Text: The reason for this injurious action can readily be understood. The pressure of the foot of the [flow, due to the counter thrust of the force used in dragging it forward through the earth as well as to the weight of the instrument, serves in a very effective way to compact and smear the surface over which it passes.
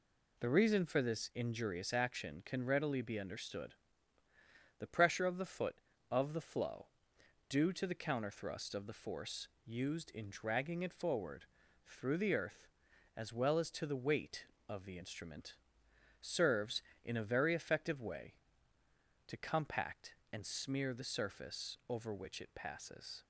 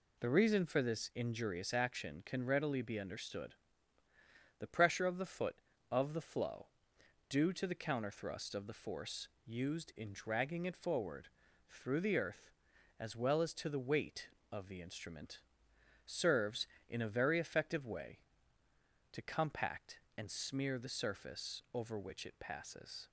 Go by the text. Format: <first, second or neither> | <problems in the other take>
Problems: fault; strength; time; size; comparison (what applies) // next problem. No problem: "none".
neither | pauses between "force" and "used"; slight; the same in both // pauses between "forward" and "through"; the same in both